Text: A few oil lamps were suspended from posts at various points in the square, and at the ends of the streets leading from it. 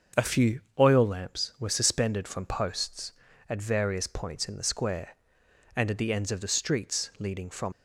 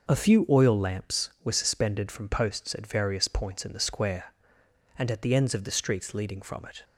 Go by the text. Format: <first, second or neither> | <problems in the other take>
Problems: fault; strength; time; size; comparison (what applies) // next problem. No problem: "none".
second | starts louder than the rest; until 1.3 s; 7 dB; noticeable in the second // pauses between "few" and "oil"; slight; at 0.6 s; 0.18 s long // stops before "it"; at 7.7 s